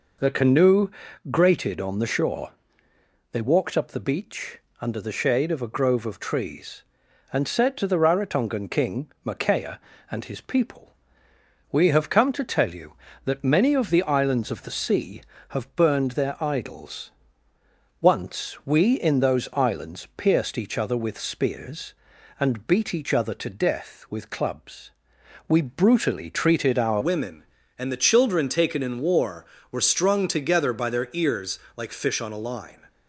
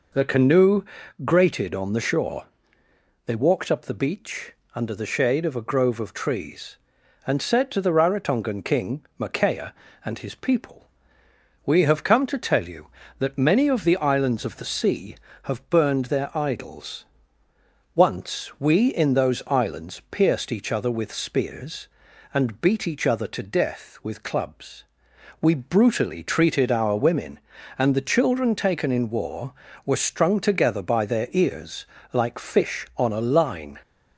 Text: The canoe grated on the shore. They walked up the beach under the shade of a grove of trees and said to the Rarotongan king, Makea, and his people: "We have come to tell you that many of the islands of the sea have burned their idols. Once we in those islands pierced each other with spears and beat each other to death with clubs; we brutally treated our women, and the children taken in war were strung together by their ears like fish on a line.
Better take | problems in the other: second | pauses between "canoe" and "grated"; at 0.9 s; 0.40 s long; also in the second // pauses between "beach" and "under"; slight; at 4.5 s; 0.22 s long; slight in the second // changes voice at "women"; from 27.0 s on; 5.8 s long // pauses between "ears" and "like"; slight; at 31.5 s; 0.18 s long; slight in the second

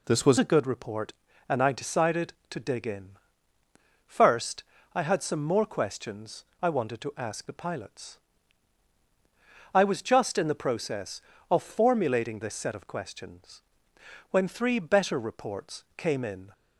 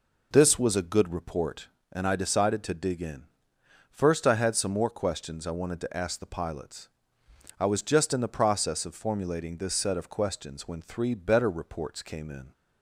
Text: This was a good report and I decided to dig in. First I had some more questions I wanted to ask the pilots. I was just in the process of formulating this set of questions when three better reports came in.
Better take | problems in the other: second | changes voice at "a"; from 0.3 s on; 16.2 s long // pauses between "First" and "I"; slight; at 4.6 s; 0.30 s long // pauses between "questions" and "I"; slight; at 6.4 s; 0.18 s long // pauses between "questions" and "when"; noticeable; at 13.6 s; 0.70 s long

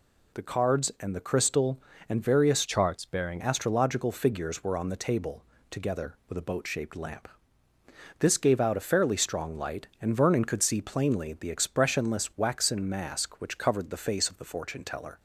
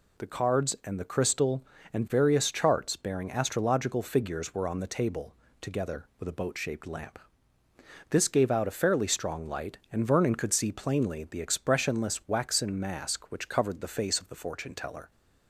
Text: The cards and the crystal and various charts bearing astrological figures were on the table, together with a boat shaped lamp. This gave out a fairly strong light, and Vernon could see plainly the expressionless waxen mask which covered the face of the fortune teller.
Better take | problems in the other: second | changes voice from "charts" to "bearing"; from 2.6 to 3.4 s; 0.8 s long

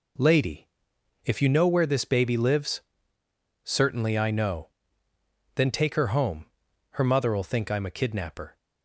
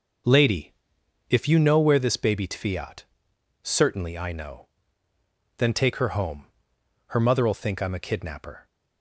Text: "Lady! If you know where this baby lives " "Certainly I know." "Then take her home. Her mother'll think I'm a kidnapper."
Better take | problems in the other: first | starts louder than the rest; noticeable; until 1.8 s; 6 dB // says "tfiat" for "lives"; at 2.4 s

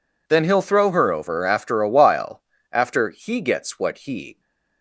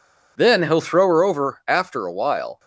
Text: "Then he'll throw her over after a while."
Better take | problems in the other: second | goes on to say "After he gets what he"; strong; from 2.7 s on; 1.6 s long

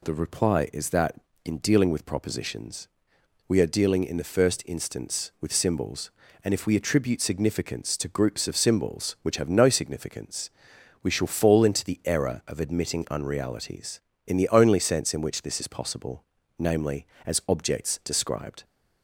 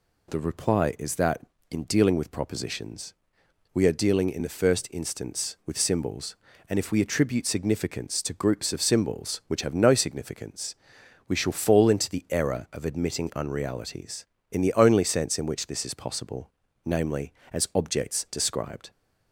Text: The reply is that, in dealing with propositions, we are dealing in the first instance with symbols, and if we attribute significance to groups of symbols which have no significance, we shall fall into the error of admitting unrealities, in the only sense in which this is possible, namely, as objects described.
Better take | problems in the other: neither | none

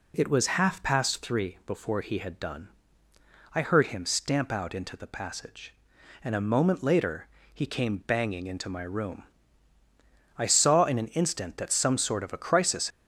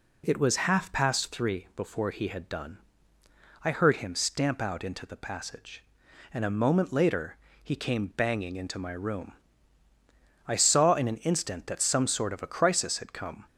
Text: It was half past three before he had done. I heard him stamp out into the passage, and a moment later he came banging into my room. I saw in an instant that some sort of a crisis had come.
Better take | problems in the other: second | pauses between "later" and "he"; slight; at 7.2 s; 0.26 s long; slight in the second // stops before "had come"; at 12.9 s

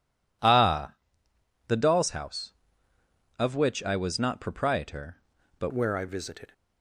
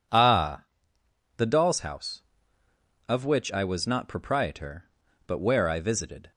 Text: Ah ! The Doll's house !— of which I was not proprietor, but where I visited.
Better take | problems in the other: second | changes voice at "where"; from 5.7 s on; 0.8 s long

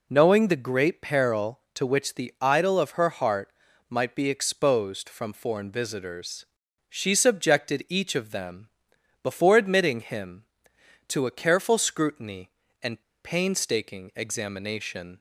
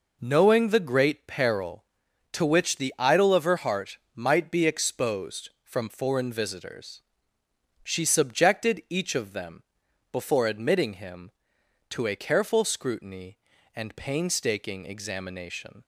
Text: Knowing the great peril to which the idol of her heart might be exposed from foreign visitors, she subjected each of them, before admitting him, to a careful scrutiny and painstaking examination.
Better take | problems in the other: second | pauses between "heart" and "might"; at 3.4 s; 0.40 s long; slight in the second // pauses between "and" and "painstaking"; slight; at 13.0 s; 0.22 s long

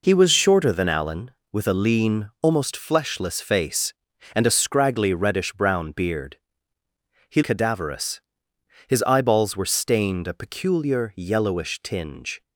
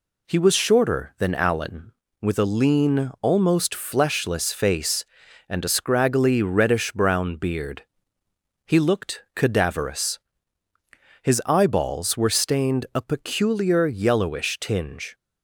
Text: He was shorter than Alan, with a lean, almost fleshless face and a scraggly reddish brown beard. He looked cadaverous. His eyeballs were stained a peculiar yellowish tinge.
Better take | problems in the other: second | skips "looked"; at 7.4 s

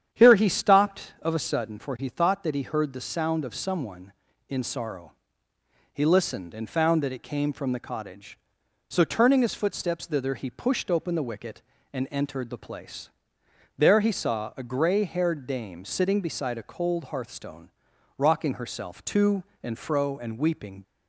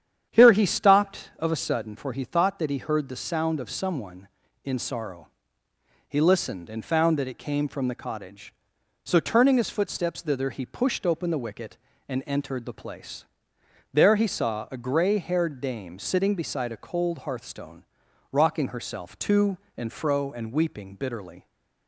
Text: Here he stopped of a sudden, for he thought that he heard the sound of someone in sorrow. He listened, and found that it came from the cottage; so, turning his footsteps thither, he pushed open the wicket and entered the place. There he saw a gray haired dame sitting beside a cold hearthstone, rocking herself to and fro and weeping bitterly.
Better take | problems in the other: second | starts louder than the rest; strong; until 1.1 s; 9 dB; strong in the second // stops before "bitterly"; at 20.8 s

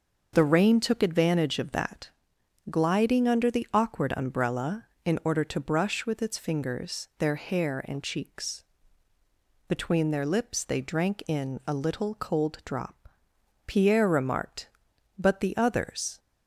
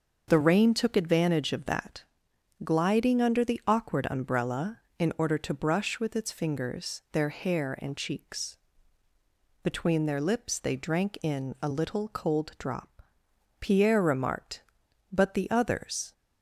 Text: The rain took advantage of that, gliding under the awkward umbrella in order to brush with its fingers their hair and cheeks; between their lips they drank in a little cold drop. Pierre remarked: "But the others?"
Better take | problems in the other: neither | starts louder than the rest; the same in both

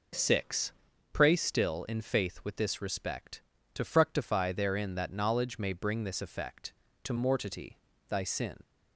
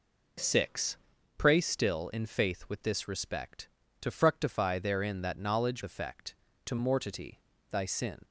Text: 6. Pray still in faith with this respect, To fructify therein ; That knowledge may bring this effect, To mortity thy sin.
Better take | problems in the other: first | skips "may bring this"; at 5.8 s // pauses between "mortity" and "thy"; slight; at 7.3 s; 0.34 s long; slight in the first

